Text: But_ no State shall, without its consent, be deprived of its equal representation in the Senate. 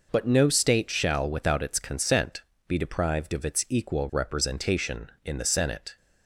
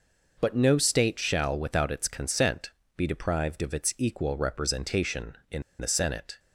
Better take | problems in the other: first | pauses between "in" and "the"; slight; at 5.6 s; 0.18 s long

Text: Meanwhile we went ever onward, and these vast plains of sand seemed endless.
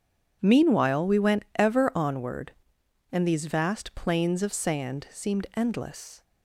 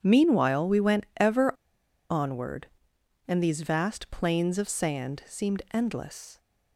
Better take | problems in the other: first | pauses between "ever" and "onward"; noticeable; at 1.5 s; 0.57 s long

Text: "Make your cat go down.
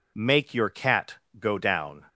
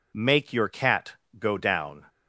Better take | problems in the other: neither | pauses between "cat" and "go"; slight; the same in both

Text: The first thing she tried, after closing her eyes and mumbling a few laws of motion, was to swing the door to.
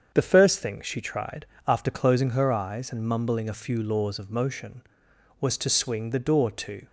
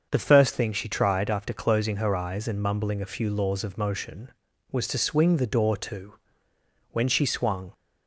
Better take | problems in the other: first | starts louder than the rest; until 1.1 s; 6.5 dB; strong in the first // goes on to say "When she swung"; noticeable; from 6.9 s on; 0.82 s long

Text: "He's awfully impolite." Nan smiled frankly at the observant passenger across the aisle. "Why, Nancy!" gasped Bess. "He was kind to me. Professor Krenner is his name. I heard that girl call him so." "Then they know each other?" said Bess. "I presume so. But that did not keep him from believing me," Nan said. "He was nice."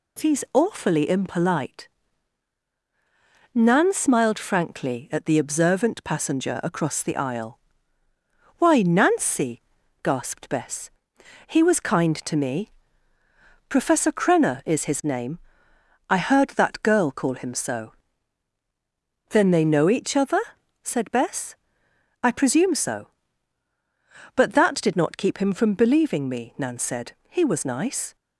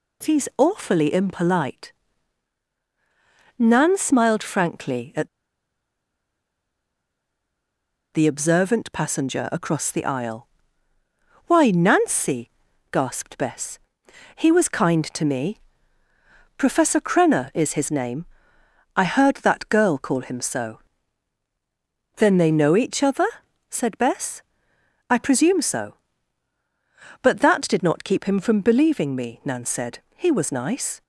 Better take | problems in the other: first | pauses between "at" and "the"; strong; at 5.2 s; 2.8 s long

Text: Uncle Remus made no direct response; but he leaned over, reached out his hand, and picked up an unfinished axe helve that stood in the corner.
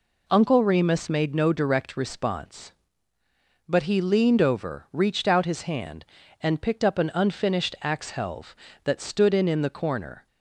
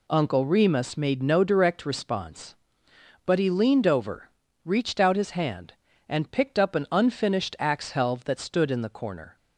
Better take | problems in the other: second | says "in" twice; at 9.4 s

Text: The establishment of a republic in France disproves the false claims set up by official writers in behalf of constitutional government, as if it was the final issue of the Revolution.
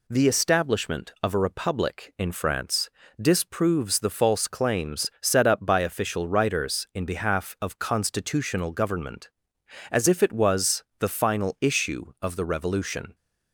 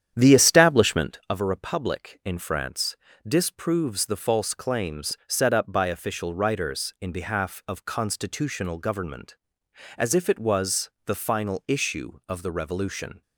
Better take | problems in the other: first | starts louder than the rest; strong; until 1.2 s; 9.5 dB // pauses between "France" and "disproves"; slight; at 2.9 s; 0.32 s long; slight in the first // pauses between "was" and "the"; slight; at 10.8 s; 0.16 s long; slight in the first

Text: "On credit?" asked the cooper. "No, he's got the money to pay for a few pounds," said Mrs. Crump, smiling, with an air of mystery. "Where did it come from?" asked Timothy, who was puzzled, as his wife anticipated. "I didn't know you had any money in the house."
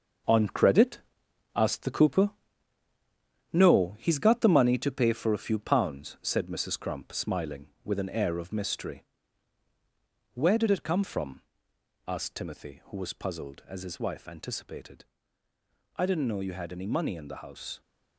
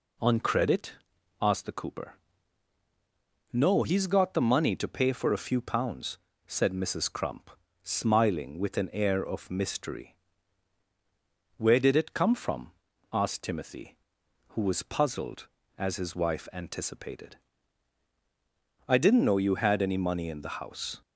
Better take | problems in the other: second | gets quieter; strong; throughout; 8 dB

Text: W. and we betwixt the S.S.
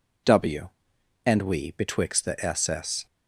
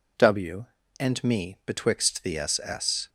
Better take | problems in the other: first | says "me" for "we"; at 1.2 s

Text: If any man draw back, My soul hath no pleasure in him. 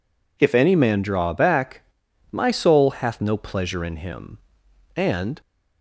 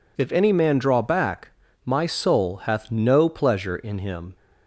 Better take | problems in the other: second | goes on to say "And"; slight; from 4.9 s on; 0.46 s long

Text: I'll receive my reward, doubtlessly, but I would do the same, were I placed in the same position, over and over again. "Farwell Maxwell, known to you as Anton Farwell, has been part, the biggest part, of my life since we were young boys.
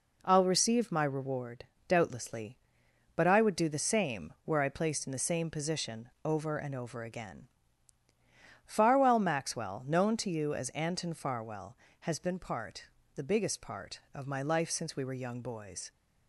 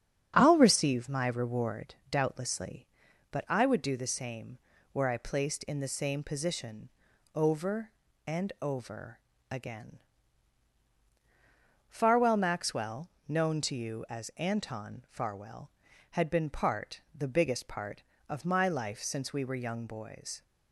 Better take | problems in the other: first | starts louder than the rest; strong; until 1.3 s; 7.5 dB // pauses between "over" and "again"; slight; at 9.2 s; 0.28 s long // says "had" for "has"; at 16.1 s

